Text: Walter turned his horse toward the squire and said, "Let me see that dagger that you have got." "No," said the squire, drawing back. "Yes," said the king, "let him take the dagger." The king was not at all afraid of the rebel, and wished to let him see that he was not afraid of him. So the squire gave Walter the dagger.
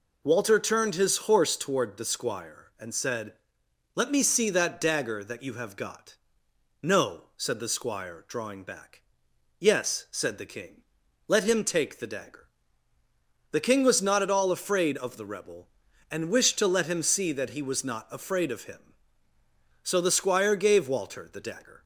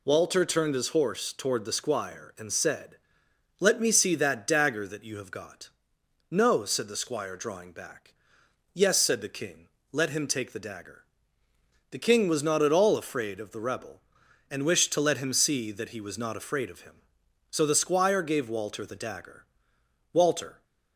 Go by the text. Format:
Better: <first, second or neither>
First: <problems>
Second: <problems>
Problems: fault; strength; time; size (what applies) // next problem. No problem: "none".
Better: first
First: none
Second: goes on to say "Walter"; from 20.1 s on; 0.52 s long